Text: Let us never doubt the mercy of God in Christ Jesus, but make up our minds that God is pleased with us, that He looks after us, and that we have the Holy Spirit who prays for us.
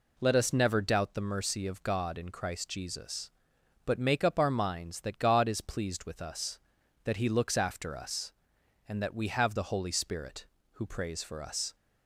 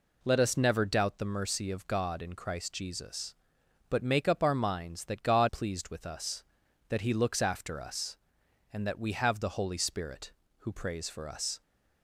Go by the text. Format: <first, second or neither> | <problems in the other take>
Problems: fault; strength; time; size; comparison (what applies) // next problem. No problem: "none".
first | skips "is"; at 5.4 s